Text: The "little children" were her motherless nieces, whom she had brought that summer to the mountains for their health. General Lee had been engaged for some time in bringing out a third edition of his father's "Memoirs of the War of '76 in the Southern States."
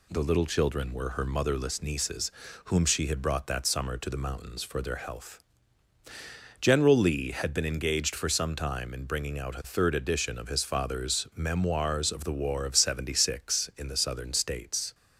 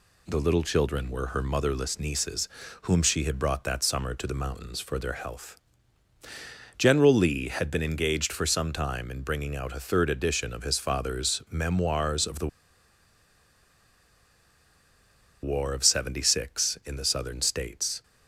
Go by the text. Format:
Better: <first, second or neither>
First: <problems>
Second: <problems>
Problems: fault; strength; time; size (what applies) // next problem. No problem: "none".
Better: first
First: none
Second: pauses between "the" and "War"; strong; at 12.4 s; 2.9 s long